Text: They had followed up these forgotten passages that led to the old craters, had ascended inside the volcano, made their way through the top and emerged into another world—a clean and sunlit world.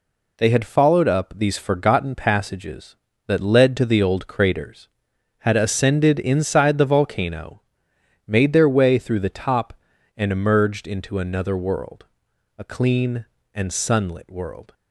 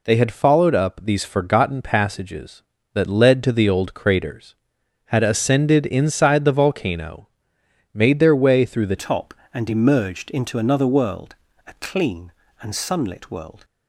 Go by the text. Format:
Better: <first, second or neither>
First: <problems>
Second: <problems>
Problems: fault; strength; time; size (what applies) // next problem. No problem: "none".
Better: first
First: none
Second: changes voice at "top"; from 8.9 s on; 4.7 s long